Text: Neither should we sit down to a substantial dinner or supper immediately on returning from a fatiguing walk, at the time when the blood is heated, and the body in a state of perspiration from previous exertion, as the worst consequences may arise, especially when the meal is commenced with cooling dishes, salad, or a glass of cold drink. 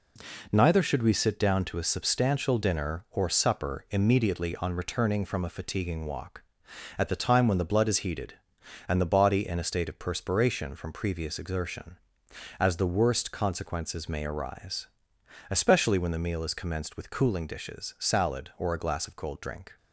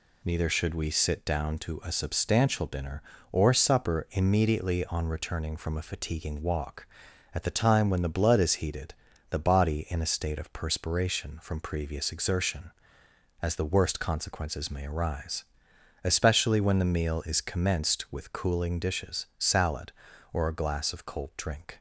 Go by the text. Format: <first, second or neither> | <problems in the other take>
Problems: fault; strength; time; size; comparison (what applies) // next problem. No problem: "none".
first | skips "and"; at 9.1 s